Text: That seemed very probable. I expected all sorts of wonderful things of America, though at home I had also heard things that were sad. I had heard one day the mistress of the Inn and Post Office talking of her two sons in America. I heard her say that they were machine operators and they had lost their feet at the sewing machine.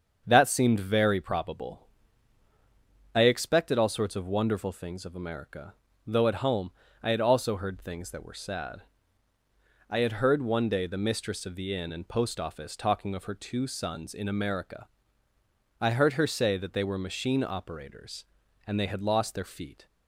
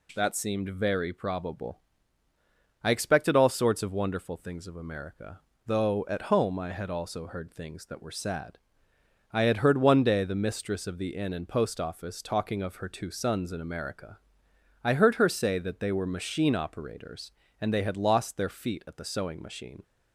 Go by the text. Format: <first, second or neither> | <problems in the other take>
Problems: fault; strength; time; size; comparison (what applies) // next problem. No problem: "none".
second | starts louder than the rest; until 1.2 s; 7 dB // pauses between "home" and "I"; slight; at 6.7 s; 0.30 s long // stops before "at the sewing machine"; at 19.8 s